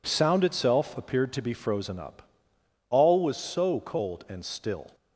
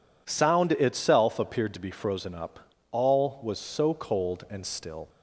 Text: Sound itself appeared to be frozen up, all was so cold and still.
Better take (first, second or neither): neither